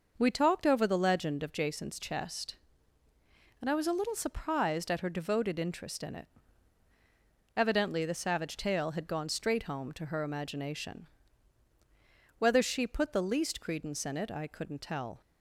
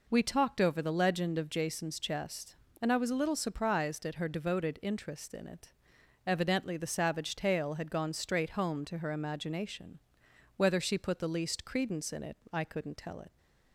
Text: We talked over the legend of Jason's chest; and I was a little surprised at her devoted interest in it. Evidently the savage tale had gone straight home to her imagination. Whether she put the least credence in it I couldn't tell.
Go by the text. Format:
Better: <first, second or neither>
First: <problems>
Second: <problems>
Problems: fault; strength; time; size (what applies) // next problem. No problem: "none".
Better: first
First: none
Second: pauses between "it" and "I"; slight; at 12.3 s; 0.16 s long // goes on to say "It"; slight; from 13.1 s on; 0.18 s long